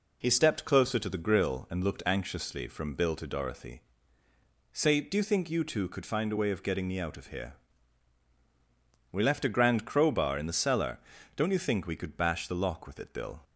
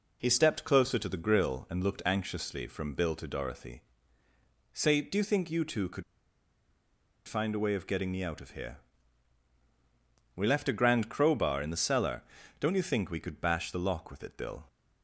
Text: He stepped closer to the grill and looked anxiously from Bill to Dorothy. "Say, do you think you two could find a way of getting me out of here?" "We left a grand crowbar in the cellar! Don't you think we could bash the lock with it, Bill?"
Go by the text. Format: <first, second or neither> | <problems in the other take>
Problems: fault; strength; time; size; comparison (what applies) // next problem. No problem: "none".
first | pauses between "could" and "find"; at 6.0 s; 1.2 s long